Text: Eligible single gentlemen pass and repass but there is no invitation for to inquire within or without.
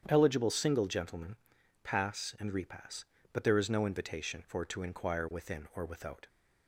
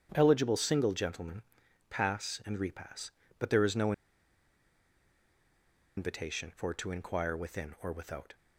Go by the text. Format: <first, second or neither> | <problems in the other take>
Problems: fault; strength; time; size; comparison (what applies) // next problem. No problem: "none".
first | starts louder than the rest; strong; until 1.1 s; 9 dB; strong in the first // pauses between "gentlemen" and "pass"; noticeable; at 1.4 s; 0.46 s long; noticeable in the first // pauses between "no" and "invitation"; strong; at 3.9 s; 2.0 s long